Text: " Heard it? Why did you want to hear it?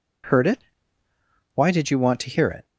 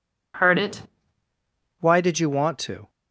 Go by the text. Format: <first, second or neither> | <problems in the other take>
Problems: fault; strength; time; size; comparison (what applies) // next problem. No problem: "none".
first | stops before "hear it"; at 2.8 s